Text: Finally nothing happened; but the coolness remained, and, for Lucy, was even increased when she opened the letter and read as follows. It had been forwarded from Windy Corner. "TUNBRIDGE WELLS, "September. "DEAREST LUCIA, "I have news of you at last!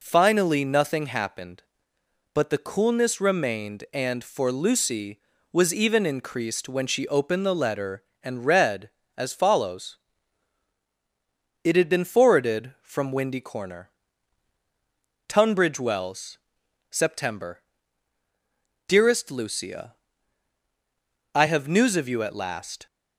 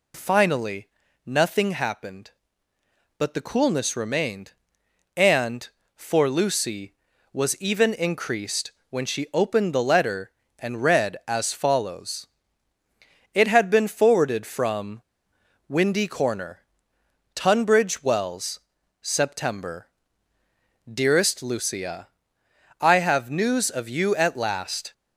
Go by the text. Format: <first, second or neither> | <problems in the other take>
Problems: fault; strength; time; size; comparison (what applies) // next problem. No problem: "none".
first | pauses between "Finally" and "nothing"; at 0.8 s; 0.38 s long // pauses between "increased" and "when"; slight; at 8.7 s; 0.18 s long // pauses between "from" and "Windy"; noticeable; at 15.0 s; 0.65 s long